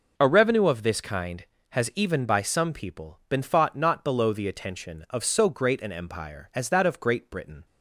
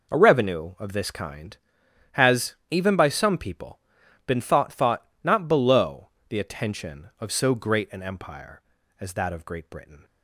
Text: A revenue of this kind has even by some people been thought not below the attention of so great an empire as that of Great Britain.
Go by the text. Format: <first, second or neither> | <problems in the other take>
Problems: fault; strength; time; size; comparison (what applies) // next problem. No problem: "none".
first | pauses between "has" and "even"; slight; at 2.5 s; 0.16 s long // pauses between "people" and "been"; noticeable; at 3.7 s; 0.48 s long // says "thought" twice; at 4.7 s // pauses between "below" and "the"; slight; at 6.0 s; 0.20 s long